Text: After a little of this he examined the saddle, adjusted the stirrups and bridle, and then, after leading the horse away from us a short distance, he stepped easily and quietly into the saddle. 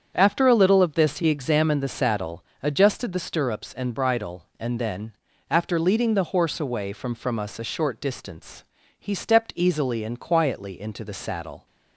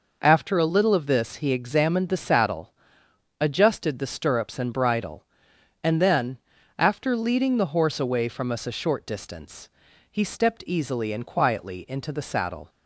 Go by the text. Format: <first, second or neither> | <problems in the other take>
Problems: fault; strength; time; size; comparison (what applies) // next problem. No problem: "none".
second | starts louder than the rest; strong; until 1.1 s; 7.5 dB // says "from" twice; at 7.1 s